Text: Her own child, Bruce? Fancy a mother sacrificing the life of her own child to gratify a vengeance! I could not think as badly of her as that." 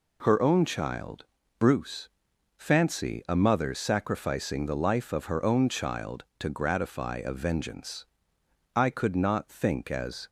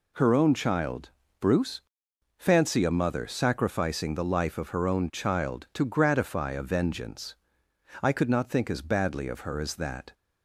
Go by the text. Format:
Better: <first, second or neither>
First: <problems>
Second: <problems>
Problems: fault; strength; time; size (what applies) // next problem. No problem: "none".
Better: second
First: stops before "badly of her as that"; at 10.2 s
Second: none